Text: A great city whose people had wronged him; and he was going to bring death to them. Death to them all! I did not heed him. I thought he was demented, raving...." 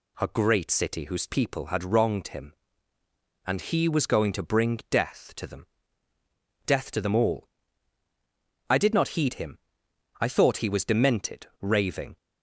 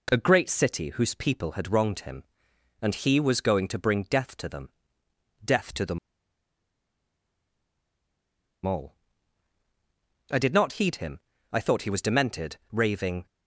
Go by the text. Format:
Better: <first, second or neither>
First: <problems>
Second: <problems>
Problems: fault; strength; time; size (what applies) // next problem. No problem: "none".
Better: first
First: none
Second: pauses between "them" and "all"; strong; at 5.9 s; 2.6 s long